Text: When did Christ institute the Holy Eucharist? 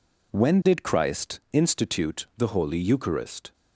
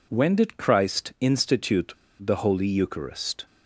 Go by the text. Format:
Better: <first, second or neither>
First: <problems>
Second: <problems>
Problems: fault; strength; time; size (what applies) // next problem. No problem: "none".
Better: first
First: none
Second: pauses between "institute" and "the"; slight; at 1.9 s; 0.25 s long